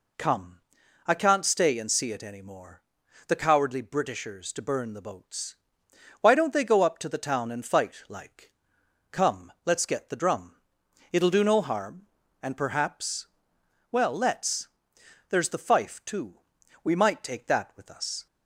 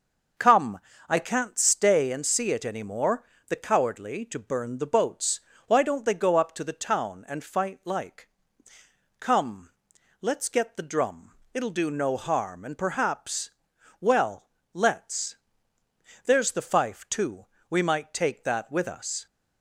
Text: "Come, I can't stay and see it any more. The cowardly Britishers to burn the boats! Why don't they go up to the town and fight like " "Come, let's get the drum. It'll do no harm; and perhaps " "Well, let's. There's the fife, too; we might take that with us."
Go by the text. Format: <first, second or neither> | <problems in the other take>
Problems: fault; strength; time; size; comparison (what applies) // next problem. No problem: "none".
first | starts louder than the rest; until 1.6 s; 6.5 dB // skips "Britishers"; at 4.2 s